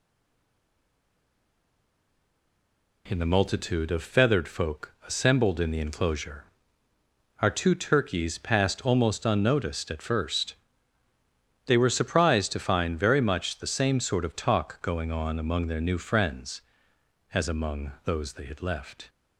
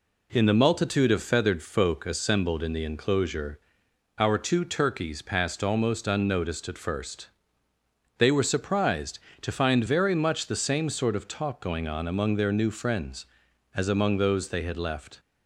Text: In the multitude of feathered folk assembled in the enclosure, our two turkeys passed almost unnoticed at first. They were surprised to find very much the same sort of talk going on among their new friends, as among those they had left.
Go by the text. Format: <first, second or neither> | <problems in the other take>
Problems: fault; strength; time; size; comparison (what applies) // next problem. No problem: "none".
second | stays silent before the first word; strong; until 3.0 s; 3.0 s long